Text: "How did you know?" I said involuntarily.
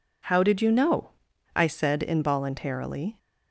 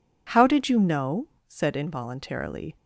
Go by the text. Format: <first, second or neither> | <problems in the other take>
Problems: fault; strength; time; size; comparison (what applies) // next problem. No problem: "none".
first | skips "I"; at 1.3 s